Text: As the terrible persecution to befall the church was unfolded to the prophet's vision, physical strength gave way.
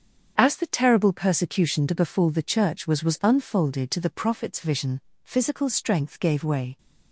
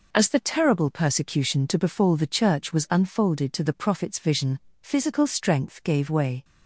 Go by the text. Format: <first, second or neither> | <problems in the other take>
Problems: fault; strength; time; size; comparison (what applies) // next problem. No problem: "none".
second | starts louder than the rest; strong; until 1.3 s; 7.5 dB // says "was" twice; at 3.0 s